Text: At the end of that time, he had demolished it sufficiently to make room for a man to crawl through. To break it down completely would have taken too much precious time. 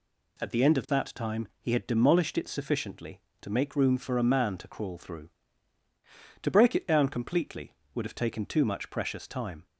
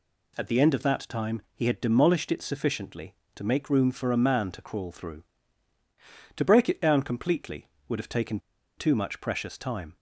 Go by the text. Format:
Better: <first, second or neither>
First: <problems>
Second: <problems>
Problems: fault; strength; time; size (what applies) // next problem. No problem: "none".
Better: first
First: none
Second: pauses between "taken" and "too"; at 8.3 s; 0.38 s long